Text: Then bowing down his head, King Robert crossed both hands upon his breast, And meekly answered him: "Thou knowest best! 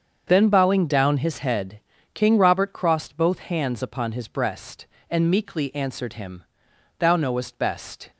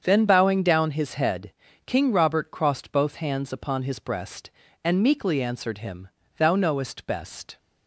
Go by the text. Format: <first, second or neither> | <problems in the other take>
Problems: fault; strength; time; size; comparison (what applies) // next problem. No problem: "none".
neither | starts louder than the rest; the same in both